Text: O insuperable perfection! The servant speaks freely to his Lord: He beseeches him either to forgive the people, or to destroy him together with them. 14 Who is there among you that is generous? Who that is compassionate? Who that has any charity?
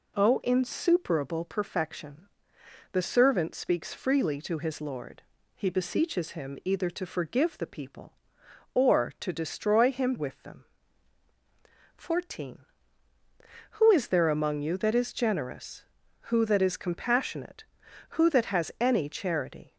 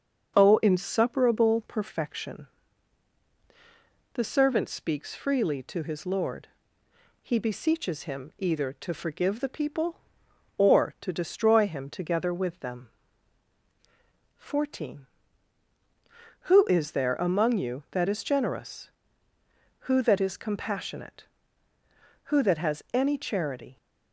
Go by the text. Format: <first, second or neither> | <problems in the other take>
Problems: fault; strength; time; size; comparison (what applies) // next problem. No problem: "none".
second | skips "together"; at 10.1 s